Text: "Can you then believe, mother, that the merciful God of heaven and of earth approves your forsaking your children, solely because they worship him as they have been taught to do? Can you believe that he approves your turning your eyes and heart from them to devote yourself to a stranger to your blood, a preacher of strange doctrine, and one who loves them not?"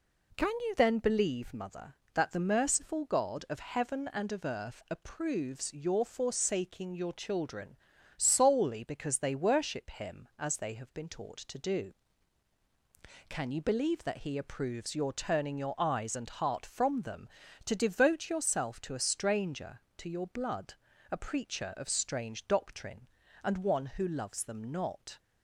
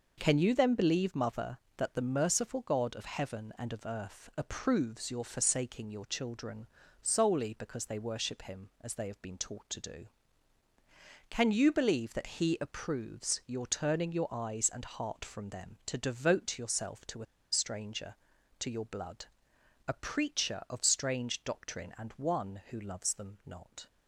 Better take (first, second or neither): first